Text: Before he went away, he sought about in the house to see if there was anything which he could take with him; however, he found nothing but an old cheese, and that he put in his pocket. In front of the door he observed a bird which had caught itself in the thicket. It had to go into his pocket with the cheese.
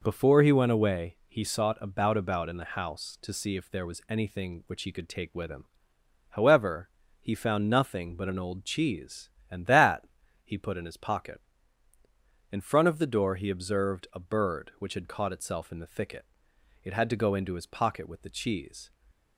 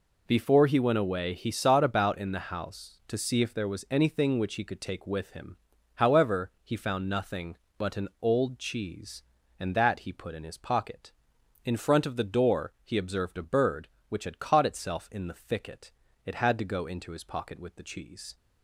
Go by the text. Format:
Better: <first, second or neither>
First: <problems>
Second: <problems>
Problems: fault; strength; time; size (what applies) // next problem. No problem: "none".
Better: second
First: says "about" twice; at 2.1 s // pauses between "that" and "he"; at 10.0 s; 0.38 s long // stays silent after the last word; slight; from 18.8 s on; 0.5 s long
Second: none